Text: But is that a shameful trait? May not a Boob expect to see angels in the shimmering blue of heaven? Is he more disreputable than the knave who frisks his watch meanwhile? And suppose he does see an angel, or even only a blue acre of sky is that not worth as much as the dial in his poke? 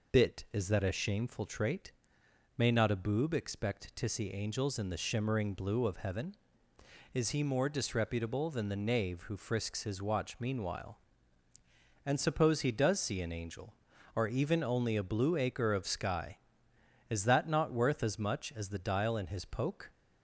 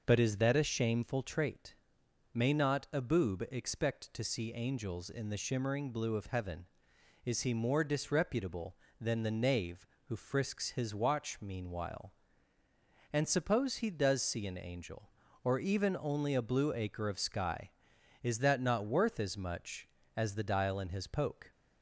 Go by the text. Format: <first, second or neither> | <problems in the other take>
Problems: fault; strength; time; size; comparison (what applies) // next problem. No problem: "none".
second | says "Bit" for "But"; at 0.1 s